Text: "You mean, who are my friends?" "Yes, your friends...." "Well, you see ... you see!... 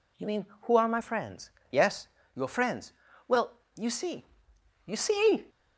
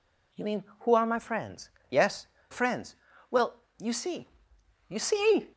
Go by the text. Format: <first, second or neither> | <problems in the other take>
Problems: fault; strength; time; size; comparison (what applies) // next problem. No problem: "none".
first | skips "your"; at 2.3 s